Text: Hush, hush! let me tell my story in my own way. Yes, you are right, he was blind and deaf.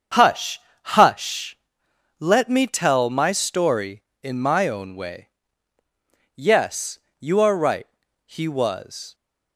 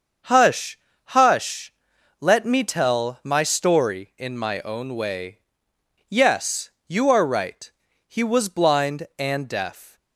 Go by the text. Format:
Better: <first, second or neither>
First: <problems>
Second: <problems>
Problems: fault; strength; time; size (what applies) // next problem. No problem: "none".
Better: second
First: starts louder than the rest; until 1.4 s; 7 dB // stops before "blind and deaf"; at 9.1 s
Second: starts louder than the rest; until 1.5 s; 6.5 dB